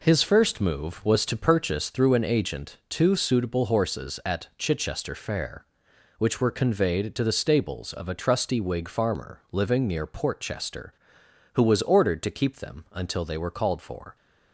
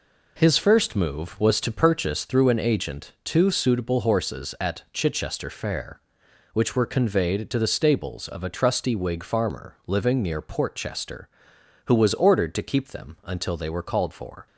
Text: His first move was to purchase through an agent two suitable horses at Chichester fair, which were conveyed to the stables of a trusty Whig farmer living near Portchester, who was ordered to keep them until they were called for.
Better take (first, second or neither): neither